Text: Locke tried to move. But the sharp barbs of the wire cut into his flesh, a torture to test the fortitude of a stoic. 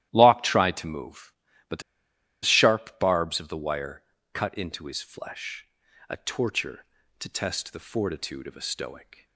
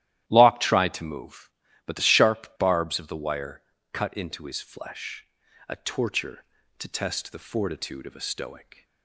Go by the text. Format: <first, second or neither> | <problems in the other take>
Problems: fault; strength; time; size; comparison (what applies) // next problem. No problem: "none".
second | starts louder than the rest; strong; until 1.1 s; 13.5 dB; strong in the second // pauses between "the" and "sharp"; noticeable; at 1.8 s; 0.63 s long // pauses between "wire" and "cut"; slight; at 4.0 s; 0.30 s long; slight in the second